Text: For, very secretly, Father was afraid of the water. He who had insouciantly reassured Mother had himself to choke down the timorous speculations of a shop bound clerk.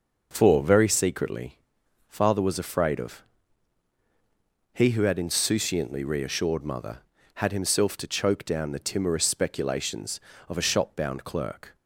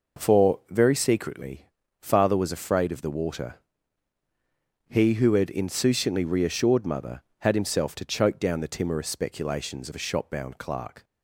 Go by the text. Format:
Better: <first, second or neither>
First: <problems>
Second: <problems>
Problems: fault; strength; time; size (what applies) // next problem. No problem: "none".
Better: second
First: skips "the water"; at 3.9 s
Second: none